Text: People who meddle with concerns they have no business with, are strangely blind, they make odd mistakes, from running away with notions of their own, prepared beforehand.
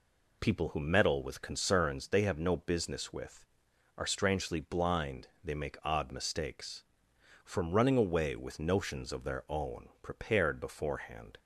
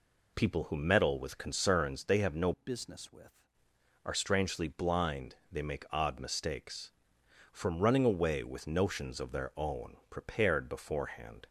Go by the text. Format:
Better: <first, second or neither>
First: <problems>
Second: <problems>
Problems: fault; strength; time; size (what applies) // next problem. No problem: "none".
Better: first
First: none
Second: changes voice from "business" to "with"; from 2.5 to 3.4 s; 0.9 s long